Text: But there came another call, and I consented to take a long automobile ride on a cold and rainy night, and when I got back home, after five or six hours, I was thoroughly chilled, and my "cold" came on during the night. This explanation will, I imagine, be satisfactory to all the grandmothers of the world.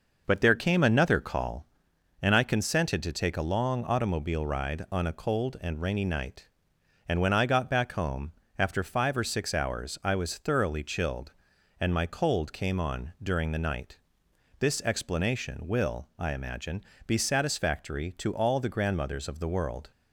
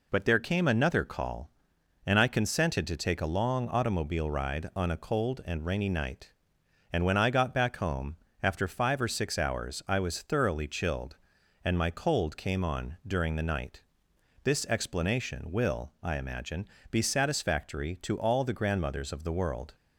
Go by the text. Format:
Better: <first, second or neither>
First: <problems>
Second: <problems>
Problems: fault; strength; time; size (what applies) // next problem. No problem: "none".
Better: second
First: starts louder than the rest; noticeable; until 1.8 s; 5.5 dB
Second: none